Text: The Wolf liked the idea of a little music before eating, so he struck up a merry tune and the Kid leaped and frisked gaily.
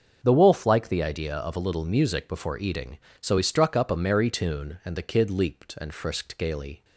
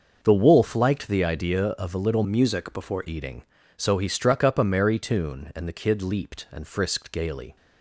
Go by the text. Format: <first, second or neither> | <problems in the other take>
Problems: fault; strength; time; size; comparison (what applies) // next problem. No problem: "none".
first | starts louder than the rest; noticeable; until 1.2 s; 6 dB; also in the first // changes voice from "music" to "before"; from 2.2 to 3.0 s; 0.8 s long